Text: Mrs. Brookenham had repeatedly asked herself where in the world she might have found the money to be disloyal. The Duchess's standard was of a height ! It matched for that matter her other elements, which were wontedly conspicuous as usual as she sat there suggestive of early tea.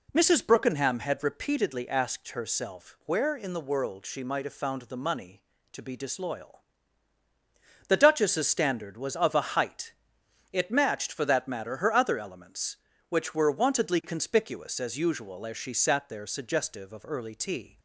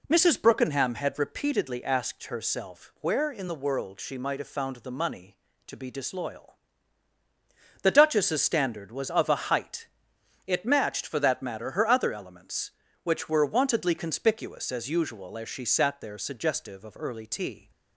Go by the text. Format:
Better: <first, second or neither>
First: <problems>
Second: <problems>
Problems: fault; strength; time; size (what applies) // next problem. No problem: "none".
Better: neither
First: none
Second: none